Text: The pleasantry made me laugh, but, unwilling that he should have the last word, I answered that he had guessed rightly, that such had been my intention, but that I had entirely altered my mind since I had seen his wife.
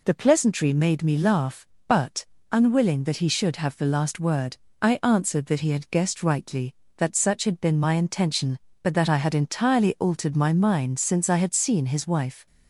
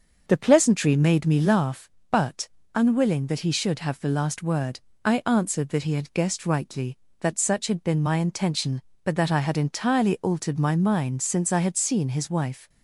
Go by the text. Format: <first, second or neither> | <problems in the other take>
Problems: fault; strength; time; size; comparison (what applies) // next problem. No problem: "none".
first | starts louder than the rest; until 1.7 s; 6.5 dB